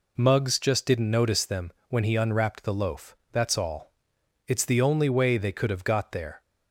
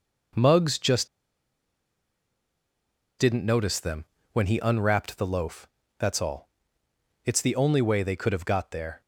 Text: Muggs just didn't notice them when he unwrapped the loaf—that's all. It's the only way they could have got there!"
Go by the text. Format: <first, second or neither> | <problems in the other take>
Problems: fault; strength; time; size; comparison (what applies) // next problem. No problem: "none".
first | pauses between "just" and "didn't"; strong; at 1.0 s; 2.1 s long // pauses between "them" and "when"; slight; at 4.0 s; 0.28 s long; slight in the first